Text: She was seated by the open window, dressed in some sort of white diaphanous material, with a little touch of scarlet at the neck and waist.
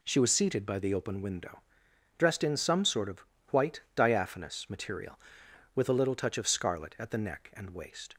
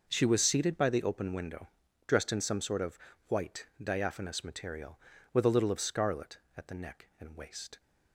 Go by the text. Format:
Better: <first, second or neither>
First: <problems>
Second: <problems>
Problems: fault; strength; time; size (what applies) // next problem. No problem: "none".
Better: first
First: pauses between "of" and "white"; slight; at 3.2 s; 0.28 s long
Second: pauses between "of" and "white"; slight; at 2.9 s; 0.30 s long // skips "touch"; at 5.7 s